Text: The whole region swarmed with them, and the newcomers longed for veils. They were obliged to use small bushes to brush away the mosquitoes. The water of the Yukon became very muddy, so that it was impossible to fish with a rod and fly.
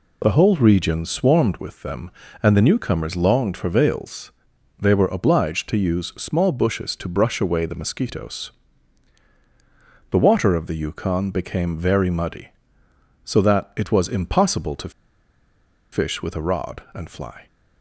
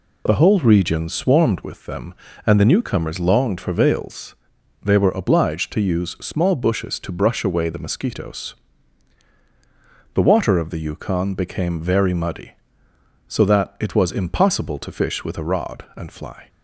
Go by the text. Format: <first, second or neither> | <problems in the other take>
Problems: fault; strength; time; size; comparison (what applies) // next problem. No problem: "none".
second | pauses between "to" and "fish"; at 14.9 s; 1.0 s long